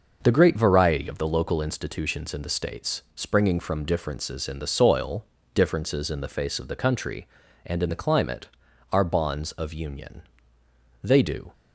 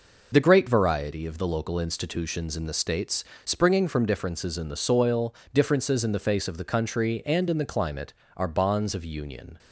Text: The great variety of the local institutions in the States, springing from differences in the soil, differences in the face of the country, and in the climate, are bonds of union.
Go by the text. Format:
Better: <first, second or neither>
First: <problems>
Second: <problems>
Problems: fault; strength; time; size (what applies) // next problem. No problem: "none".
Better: second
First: goes on to say "They do"; from 11.0 s on; 0.50 s long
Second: none